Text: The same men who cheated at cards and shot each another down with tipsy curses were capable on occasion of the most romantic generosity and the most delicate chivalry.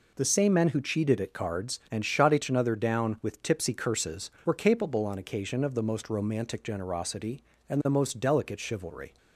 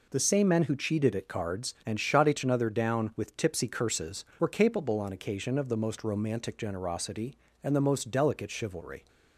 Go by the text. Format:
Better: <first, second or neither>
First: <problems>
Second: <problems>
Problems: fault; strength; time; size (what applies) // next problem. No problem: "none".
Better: neither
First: none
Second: none